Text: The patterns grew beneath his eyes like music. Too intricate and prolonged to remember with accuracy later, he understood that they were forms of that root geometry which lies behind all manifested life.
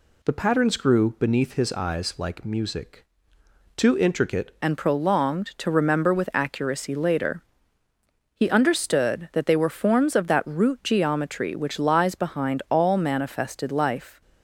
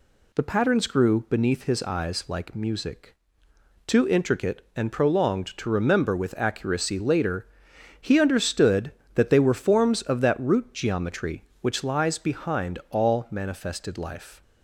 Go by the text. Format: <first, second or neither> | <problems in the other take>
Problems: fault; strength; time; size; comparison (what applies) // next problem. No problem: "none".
second | changes voice at "and"; from 4.6 s on; 9.6 s long